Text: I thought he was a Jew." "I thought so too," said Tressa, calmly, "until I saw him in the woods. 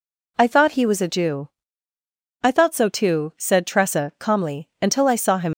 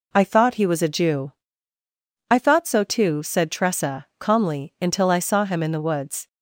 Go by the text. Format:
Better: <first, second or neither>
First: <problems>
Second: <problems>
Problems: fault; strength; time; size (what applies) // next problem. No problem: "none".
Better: second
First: stops before "in the woods"; at 5.5 s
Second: none